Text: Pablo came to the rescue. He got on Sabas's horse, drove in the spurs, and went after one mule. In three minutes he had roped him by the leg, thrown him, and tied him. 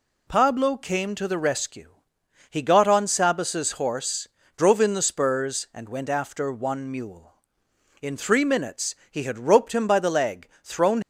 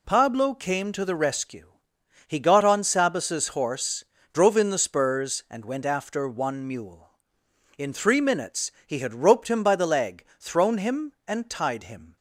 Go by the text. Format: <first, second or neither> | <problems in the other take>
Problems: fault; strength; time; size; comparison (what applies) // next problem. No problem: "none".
second | pauses between "minutes" and "he"; slight; at 8.9 s; 0.16 s long; slight in the second // stops before "him and tied him"; at 11.0 s